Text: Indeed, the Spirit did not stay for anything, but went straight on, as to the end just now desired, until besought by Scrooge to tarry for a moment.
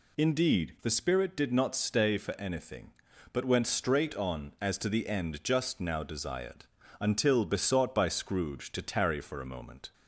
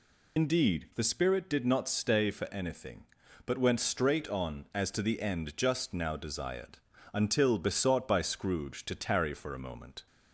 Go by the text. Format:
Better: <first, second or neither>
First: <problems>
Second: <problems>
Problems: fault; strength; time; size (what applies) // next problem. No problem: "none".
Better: first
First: none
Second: loses the start of "Indeed"; at 0.3 s; 65 ms